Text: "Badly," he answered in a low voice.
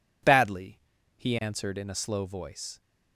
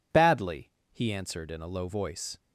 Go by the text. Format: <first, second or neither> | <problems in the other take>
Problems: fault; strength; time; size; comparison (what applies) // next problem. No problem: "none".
second | says "slow" for "low"; at 1.9 s